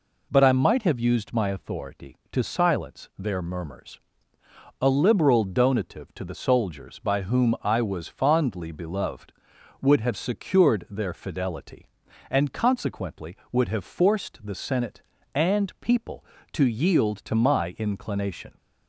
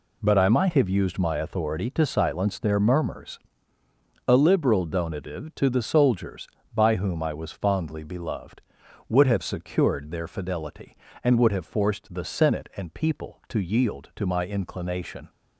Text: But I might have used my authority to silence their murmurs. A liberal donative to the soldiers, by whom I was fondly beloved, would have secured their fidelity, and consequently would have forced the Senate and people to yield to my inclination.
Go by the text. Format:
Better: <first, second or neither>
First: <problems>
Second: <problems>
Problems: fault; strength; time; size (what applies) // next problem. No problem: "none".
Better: first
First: none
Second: skips "consequently"; at 11.3 s